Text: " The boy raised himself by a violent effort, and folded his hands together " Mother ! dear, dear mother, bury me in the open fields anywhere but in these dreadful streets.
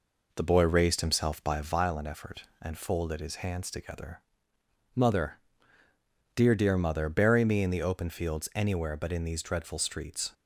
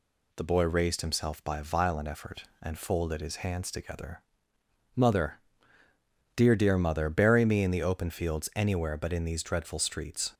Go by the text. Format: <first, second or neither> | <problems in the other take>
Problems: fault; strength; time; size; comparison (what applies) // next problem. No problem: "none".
second | starts louder than the rest; noticeable; until 1.8 s; 4.5 dB